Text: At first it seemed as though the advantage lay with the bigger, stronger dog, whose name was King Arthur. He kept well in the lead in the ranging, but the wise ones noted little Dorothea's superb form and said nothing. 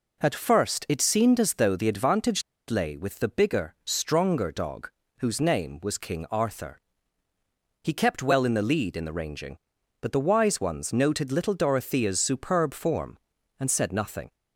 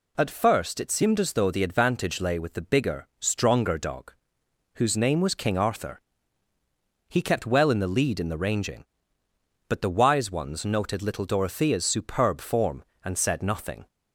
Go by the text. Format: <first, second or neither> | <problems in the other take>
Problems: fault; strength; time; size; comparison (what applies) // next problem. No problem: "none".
second | pauses between "advantage" and "lay"; slight; at 2.4 s; 0.27 s long